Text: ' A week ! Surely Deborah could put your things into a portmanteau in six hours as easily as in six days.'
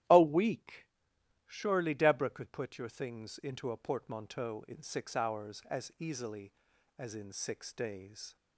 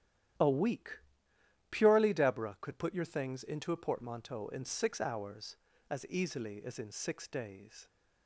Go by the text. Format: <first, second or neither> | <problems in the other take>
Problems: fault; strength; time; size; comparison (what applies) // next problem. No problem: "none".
first | starts louder than the rest; strong; until 2.0 s; 11 dB; strong in the first // says "Purely" for "Surely"; at 1.7 s